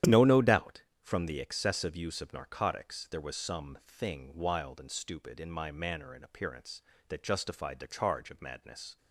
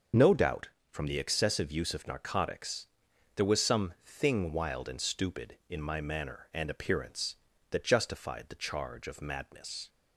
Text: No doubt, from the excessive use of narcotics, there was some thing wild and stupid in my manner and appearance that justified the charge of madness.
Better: second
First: starts louder than the rest; strong; until 1.2 s; 10.5 dB // says "No" twice; at 0.2 s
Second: starts louder than the rest; until 1.3 s; 6.5 dB

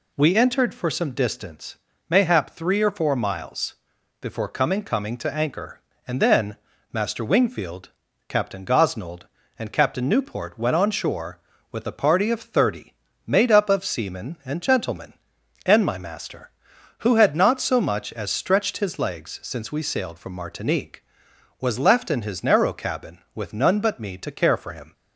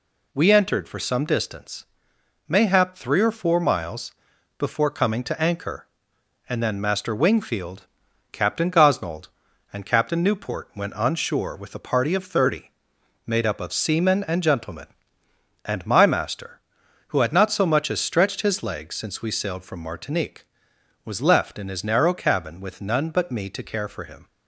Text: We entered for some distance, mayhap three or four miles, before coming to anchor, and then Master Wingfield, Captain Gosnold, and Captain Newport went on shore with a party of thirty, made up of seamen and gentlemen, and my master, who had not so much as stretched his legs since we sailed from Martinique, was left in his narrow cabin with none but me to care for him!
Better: second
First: says "coming" twice; at 4.8 s // pauses between "then" and "Master"; slight; at 6.5 s; 0.36 s long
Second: none

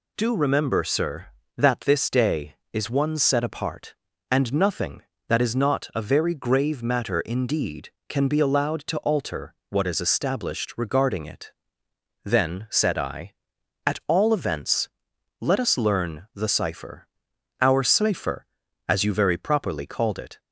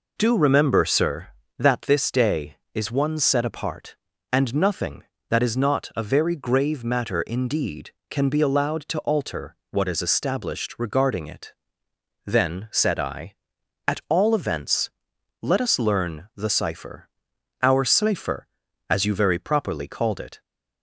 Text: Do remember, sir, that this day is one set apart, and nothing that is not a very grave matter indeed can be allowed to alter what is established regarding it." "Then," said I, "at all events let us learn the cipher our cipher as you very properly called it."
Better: first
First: pauses between "alter" and "what"; slight; at 9.5 s; 0.16 s long // pauses between "events" and "let"; noticeable; at 14.8 s; 0.54 s long // pauses between "cipher" and "our"; noticeable; at 17.0 s; 0.50 s long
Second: starts louder than the rest; noticeable; until 1.2 s; 4.5 dB // pauses between "alter" and "what"; slight; at 9.5 s; 0.16 s long // pauses between "events" and "let"; noticeable; at 14.8 s; 0.54 s long // pauses between "cipher" and "our"; noticeable; at 17.1 s; 0.50 s long

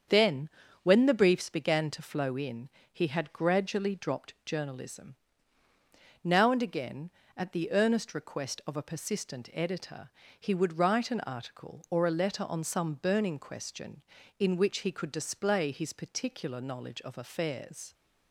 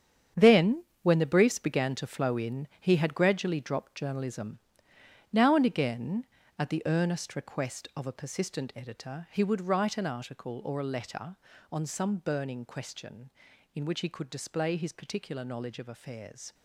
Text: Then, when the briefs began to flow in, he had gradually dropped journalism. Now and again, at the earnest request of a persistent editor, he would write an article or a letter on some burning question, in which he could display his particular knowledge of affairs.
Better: first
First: starts louder than the rest; strong; until 1.4 s; 7.5 dB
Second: gets quieter; strong; throughout; 11 dB // starts louder than the rest; strong; until 1.5 s; 8.5 dB

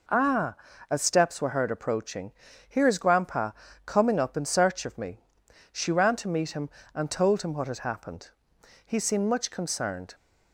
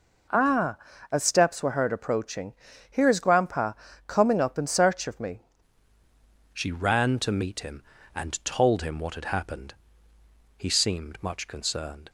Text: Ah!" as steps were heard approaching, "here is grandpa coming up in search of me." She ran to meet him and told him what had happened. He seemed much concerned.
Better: first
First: pauses between "grandpa" and "coming"; slight; at 3.5 s; 0.34 s long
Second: pauses between "grandpa" and "coming"; slight; at 3.7 s; 0.34 s long // changes voice at "She"; from 6.5 s on; 5.5 s long

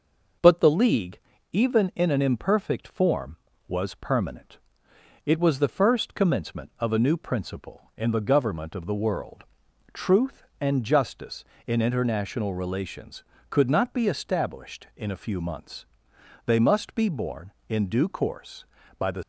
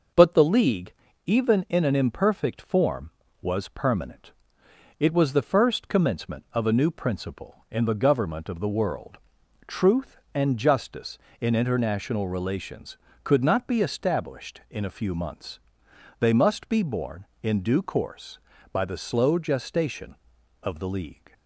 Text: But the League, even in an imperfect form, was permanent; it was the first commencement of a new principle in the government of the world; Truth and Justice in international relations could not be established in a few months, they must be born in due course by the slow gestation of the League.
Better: second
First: stops before "slow gestation of the League"; at 19.2 s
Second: none

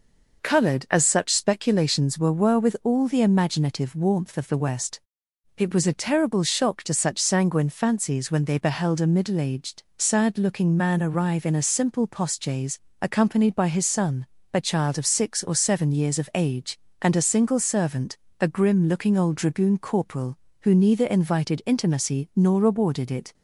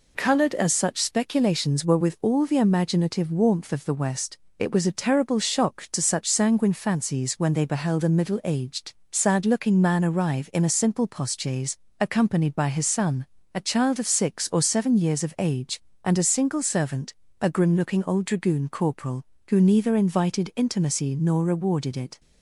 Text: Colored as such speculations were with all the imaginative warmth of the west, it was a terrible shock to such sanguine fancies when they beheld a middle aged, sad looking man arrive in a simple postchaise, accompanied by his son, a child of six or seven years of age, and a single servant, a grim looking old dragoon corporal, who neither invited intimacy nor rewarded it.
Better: second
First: says "were" twice; at 2.3 s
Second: none

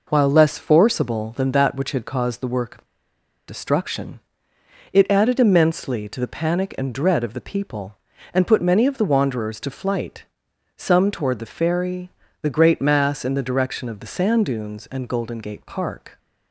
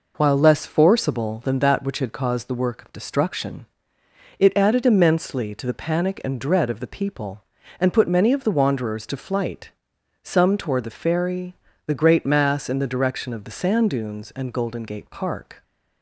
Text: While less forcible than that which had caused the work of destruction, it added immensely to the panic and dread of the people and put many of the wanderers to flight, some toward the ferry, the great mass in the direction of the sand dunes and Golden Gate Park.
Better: second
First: pauses between "of" and "destruction"; noticeable; at 2.8 s; 0.62 s long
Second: none

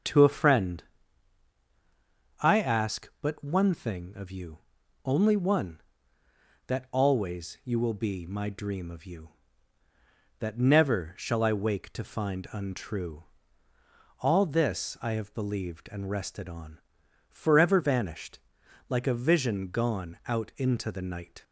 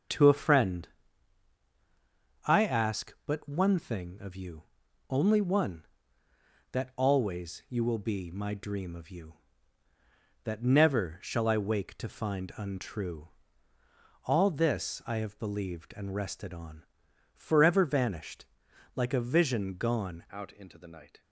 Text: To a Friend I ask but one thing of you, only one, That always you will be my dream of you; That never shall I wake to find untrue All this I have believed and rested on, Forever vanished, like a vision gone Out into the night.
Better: first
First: starts louder than the rest; until 2.6 s; 7 dB // pauses between "Friend" and "I"; strong; at 0.8 s; 1.5 s long // pauses between "untrue" and "All"; noticeable; at 13.2 s; 0.96 s long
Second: starts louder than the rest; until 2.6 s; 7 dB // pauses between "Friend" and "I"; strong; at 0.8 s; 1.5 s long // pauses between "untrue" and "All"; noticeable; at 13.2 s; 0.96 s long // changes voice at "Out"; from 20.3 s on; 0.9 s long

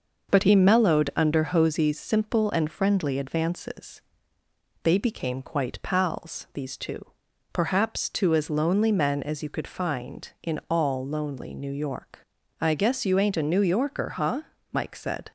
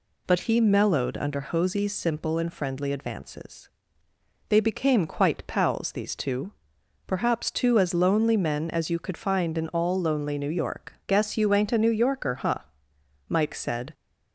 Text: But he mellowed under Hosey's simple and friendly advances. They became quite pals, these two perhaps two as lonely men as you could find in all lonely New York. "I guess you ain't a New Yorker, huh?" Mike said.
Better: first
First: pauses between "two" and "perhaps"; noticeable; at 7.0 s; 0.46 s long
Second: pauses between "two" and "perhaps"; noticeable; at 6.5 s; 0.56 s long // skips "I"; at 11.0 s

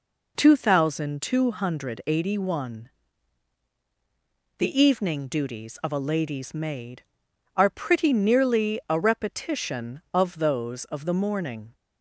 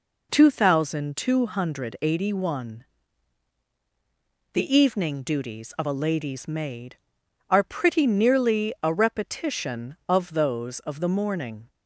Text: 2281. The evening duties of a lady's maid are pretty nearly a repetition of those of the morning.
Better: neither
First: none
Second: none

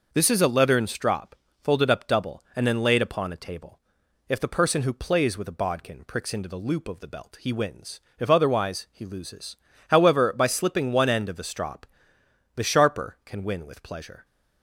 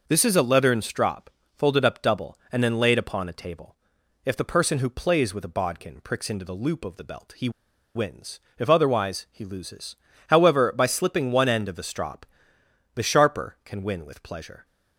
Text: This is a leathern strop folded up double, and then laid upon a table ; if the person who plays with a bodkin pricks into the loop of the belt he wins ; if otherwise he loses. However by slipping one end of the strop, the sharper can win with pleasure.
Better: first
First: pauses between "strop" and "folded"; slight; at 1.3 s; 0.26 s long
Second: pauses between "strop" and "folded"; slight; at 1.3 s; 0.26 s long // pauses between "he" and "wins"; at 7.4 s; 0.45 s long

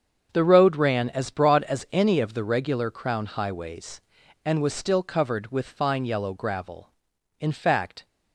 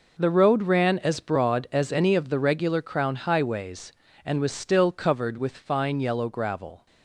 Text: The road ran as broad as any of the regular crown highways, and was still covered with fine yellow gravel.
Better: second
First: starts louder than the rest; until 1.3 s; 7 dB // goes on to say "In fact"; noticeable; from 7.3 s on; 0.68 s long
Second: none

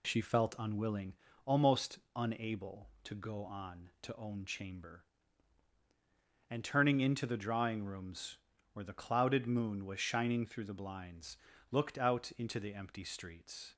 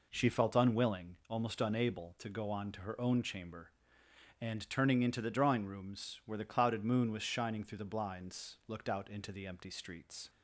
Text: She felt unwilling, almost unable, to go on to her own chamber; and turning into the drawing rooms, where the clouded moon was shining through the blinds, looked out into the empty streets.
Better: second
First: pauses between "almost" and "unable"; slight; at 1.9 s; 0.16 s long // skips "her"; at 4.1 s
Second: none

